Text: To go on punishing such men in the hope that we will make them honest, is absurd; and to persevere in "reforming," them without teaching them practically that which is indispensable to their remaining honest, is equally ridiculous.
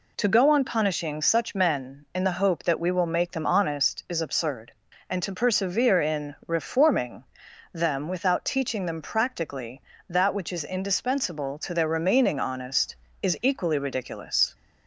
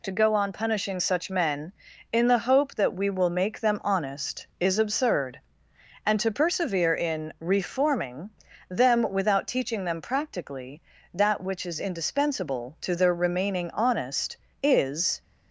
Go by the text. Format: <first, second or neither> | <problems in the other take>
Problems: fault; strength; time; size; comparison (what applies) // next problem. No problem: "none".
first | stops before "equally ridiculous"; at 15.2 s